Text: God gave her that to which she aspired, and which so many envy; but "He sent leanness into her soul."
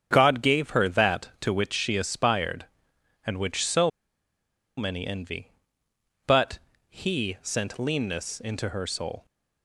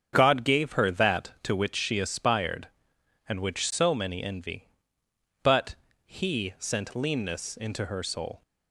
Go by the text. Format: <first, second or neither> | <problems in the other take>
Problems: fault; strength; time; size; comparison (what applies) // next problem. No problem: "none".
second | starts louder than the rest; strong; until 1.1 s; 8 dB; strong in the second // pauses between "so" and "many"; noticeable; at 3.8 s; 0.87 s long // pauses between "but" and "He"; slight; at 6.5 s; 0.30 s long; slight in the second